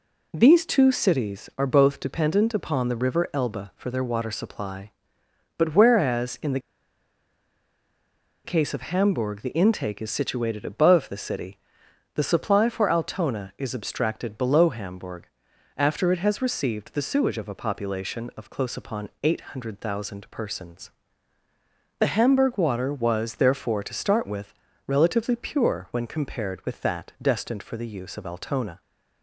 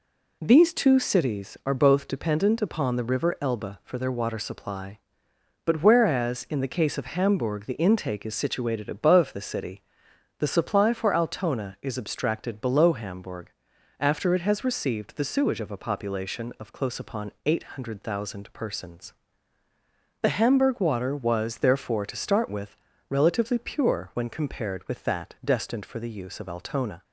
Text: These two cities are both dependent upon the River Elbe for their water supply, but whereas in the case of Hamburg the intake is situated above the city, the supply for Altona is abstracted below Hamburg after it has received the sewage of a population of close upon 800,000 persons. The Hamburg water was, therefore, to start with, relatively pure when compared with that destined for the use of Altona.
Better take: second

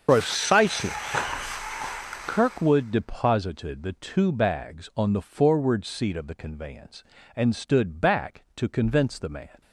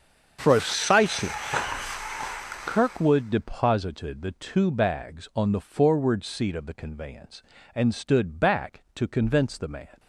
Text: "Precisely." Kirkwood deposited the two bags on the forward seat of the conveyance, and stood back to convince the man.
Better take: second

